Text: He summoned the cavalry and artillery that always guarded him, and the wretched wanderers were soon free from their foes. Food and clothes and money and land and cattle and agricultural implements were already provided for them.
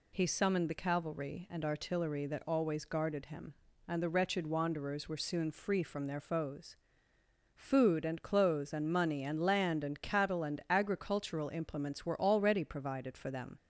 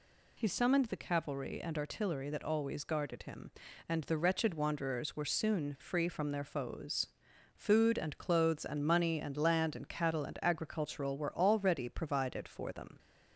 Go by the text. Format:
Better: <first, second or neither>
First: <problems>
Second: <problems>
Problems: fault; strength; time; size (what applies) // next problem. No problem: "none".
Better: first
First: none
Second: skips "implements"; at 11.1 s